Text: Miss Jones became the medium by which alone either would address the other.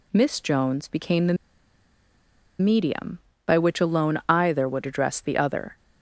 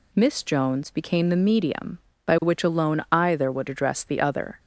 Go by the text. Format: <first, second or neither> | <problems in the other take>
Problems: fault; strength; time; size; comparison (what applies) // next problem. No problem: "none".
second | pauses between "the" and "medium"; strong; at 1.3 s; 1.2 s long